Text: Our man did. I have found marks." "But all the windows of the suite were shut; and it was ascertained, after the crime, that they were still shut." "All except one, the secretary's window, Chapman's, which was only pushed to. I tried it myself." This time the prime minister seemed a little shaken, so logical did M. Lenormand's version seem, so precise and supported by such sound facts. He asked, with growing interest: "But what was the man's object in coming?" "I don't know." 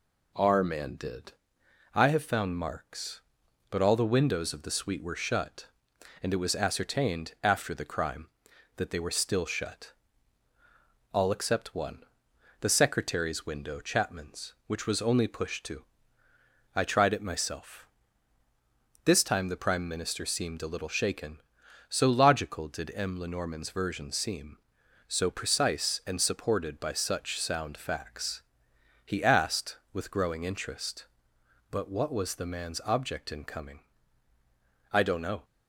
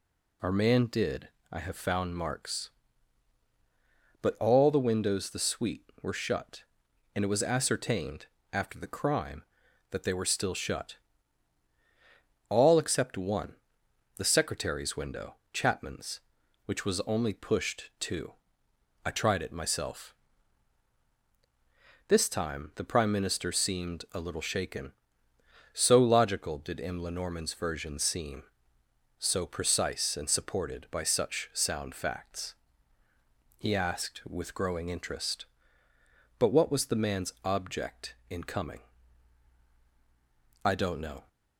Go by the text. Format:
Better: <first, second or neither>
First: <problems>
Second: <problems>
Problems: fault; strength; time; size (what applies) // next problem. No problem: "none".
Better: first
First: none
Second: skips "of"; at 5.2 s